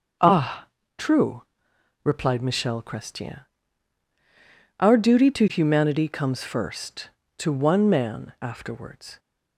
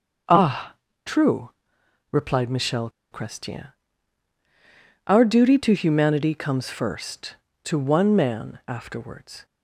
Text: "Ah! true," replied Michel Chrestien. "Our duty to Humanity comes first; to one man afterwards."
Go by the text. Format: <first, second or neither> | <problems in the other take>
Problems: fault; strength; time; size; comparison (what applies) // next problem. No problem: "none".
first | starts louder than the rest; until 2.2 s; 6.5 dB; also in the first // pauses between "Michel" and "Chrestien"; slight; at 2.8 s; 0.22 s long